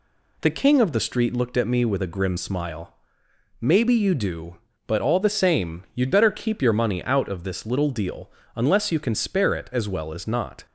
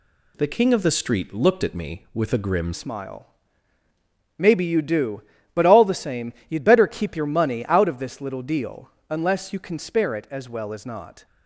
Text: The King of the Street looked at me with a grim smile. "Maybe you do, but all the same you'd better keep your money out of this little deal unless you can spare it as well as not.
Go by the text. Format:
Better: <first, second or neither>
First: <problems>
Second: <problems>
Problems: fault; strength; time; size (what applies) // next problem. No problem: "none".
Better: first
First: pauses between "deal" and "unless"; slight; at 8.2 s; 0.26 s long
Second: changes voice at "smile"; from 2.7 s on; 8.5 s long // pauses between "same" and "you'd"; slight; at 6.3 s; 0.16 s long // pauses between "deal" and "unless"; slight; at 8.8 s; 0.18 s long